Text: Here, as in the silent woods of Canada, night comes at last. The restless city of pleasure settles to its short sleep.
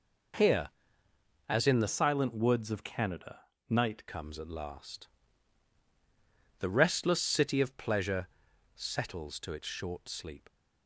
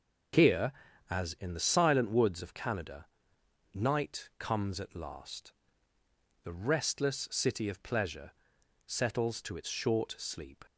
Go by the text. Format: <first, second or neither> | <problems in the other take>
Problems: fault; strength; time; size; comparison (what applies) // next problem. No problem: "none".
second | changes voice from "silent" to "night"; from 1.8 to 4.0 s; 2.2 s long // pauses between "pleasure" and "settles"; noticeable; at 8.2 s; 0.46 s long; noticeable in the second